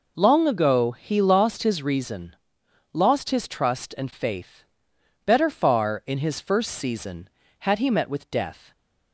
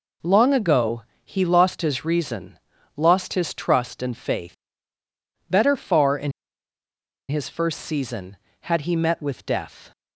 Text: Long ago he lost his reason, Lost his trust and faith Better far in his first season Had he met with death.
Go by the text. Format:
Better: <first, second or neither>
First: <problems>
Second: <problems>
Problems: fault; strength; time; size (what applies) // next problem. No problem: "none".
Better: first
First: pauses between "faith" and "Better"; noticeable; at 4.6 s; 0.62 s long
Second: pauses between "ago" and "he"; slight; at 1.0 s; 0.22 s long // pauses between "faith" and "Better"; noticeable; at 4.5 s; 0.94 s long // pauses between "in" and "his"; noticeable; at 6.3 s; 0.97 s long